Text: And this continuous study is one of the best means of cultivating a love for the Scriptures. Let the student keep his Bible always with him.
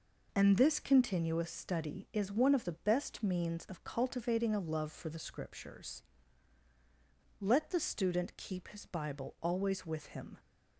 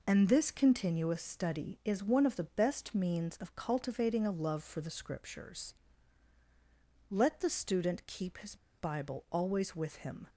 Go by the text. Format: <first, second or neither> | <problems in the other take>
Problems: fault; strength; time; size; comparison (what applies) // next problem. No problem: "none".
first | pauses between "his" and "Bible"; slight; at 8.5 s; 0.22 s long